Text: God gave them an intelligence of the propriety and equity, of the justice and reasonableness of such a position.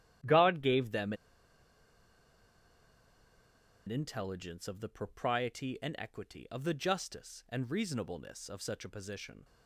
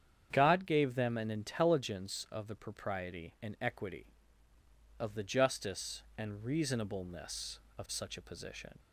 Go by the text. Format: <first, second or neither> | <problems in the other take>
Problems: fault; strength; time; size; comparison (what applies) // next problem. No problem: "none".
second | starts louder than the rest; strong; until 3.9 s; 11.5 dB; strong in the second // pauses between "them" and "an"; strong; at 1.1 s; 2.7 s long